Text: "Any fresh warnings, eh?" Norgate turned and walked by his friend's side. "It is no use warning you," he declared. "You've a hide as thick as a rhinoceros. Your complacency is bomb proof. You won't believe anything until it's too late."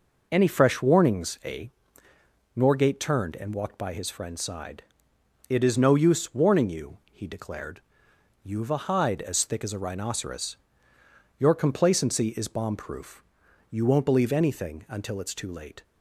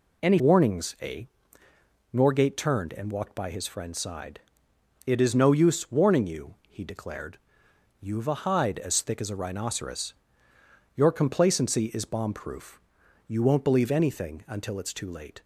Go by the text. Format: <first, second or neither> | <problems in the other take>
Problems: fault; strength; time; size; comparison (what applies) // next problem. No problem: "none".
first | skips "fresh"; at 0.3 s